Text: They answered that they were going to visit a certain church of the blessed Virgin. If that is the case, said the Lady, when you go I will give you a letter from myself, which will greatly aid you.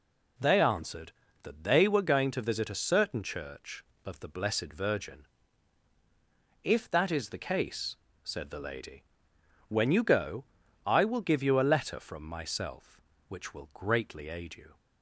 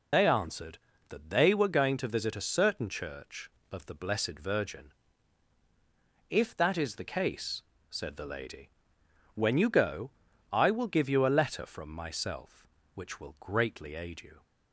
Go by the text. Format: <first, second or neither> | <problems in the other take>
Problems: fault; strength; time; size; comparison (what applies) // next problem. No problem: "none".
first | loses the start of "They"; at 0.1 s; 85 ms // pauses between "go" and "I"; at 10.1 s; 0.40 s long; also in the first